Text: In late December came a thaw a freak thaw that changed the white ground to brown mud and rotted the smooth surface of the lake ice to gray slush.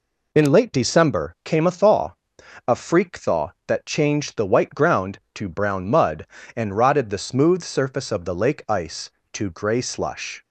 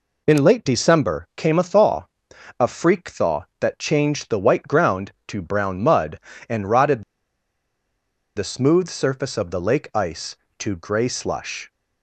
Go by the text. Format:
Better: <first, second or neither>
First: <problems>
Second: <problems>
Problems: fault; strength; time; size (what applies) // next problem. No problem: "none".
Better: first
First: pauses between "thaw" and "a"; noticeable; at 2.1 s; 0.52 s long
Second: pauses between "thaw" and "a"; noticeable; at 2.0 s; 0.52 s long // pauses between "rotted" and "the"; strong; at 7.0 s; 1.3 s long